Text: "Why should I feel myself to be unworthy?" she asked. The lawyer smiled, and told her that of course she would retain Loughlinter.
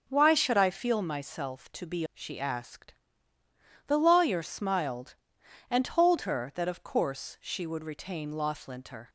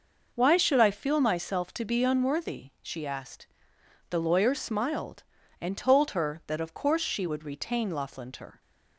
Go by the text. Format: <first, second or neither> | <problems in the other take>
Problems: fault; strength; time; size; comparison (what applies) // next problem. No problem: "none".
second | skips "unworthy"; at 2.0 s